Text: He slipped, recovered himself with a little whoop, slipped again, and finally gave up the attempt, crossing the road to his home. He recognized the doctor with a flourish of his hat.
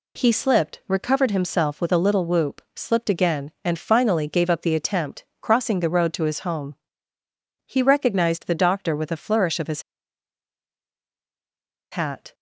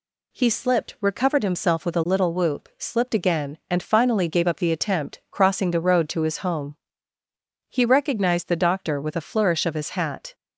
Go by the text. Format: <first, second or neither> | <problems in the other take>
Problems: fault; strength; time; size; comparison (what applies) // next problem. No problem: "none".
second | pauses between "his" and "hat"; strong; at 9.8 s; 2.0 s long